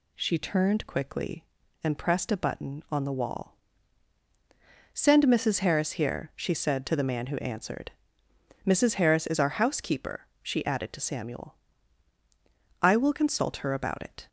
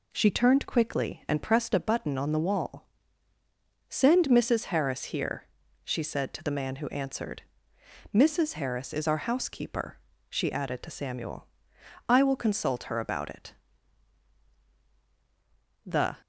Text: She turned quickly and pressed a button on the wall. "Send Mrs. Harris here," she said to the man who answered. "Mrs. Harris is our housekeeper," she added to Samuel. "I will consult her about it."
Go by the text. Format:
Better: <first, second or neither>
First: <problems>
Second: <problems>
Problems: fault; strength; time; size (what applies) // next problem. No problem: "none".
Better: first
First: none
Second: goes on to say "The"; slight; from 15.8 s on; 0.32 s long